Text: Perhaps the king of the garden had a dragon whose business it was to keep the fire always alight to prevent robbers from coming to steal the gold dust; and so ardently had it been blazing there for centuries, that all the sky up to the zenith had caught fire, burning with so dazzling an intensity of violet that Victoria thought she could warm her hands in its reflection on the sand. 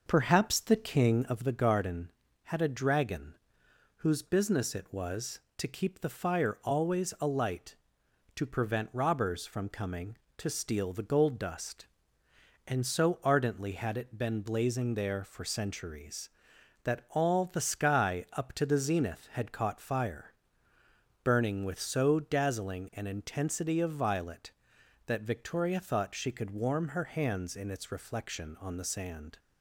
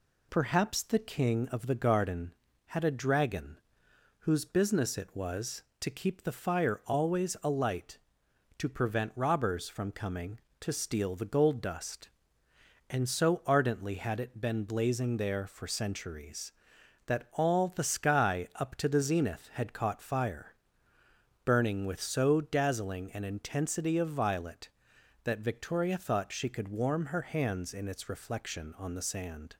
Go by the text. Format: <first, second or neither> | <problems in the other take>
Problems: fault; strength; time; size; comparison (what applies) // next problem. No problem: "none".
second | starts louder than the rest; noticeable; until 1.5 s; 5.5 dB // pauses between "dragon" and "whose"; noticeable; at 3.3 s; 0.62 s long; noticeable in the second